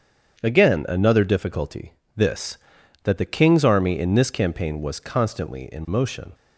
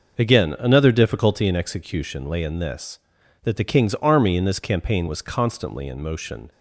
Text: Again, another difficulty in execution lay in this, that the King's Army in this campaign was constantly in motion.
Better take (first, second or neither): second